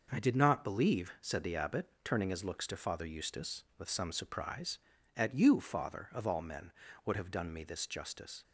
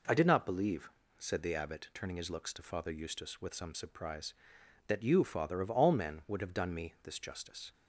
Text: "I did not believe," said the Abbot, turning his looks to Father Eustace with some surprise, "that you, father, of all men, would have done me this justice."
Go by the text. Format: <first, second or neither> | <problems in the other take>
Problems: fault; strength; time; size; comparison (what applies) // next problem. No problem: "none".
second | says "at" for "that"; at 5.1 s